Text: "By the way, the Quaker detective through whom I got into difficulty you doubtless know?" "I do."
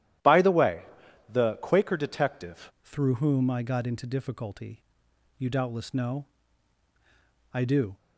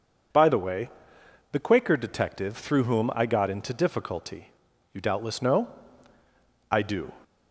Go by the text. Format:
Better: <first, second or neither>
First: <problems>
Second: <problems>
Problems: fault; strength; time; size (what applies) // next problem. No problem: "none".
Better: second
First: starts louder than the rest; strong; until 1.7 s; 12.5 dB // changes voice at "through"; from 2.8 s on; 5.1 s long // pauses between "difficulty" and "you"; noticeable; at 4.8 s; 0.56 s long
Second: pauses between "difficulty" and "you"; at 4.5 s; 0.42 s long